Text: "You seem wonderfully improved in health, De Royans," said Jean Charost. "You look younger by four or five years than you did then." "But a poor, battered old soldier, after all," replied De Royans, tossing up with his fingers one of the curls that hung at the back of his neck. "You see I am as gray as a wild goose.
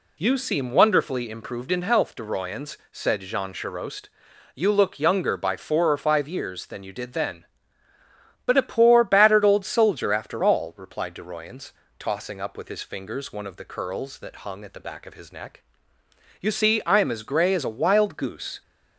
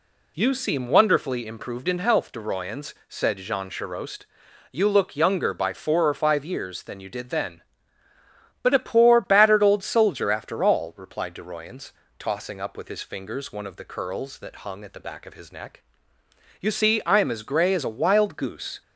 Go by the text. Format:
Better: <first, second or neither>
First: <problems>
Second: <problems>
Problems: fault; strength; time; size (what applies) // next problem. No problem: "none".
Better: neither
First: none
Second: none